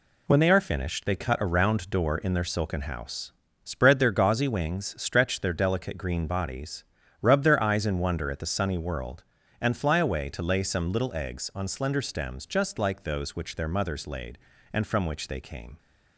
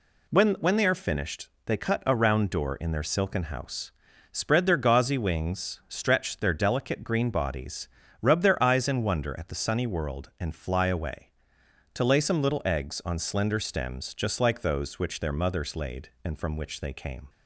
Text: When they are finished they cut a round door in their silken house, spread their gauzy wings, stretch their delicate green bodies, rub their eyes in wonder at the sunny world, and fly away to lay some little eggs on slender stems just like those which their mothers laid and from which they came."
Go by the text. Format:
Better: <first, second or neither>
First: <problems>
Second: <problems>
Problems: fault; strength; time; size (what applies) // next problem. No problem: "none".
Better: first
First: none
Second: says "When" twice; at 0.5 s // pauses between "finished" and "they"; slight; at 1.4 s; 0.18 s long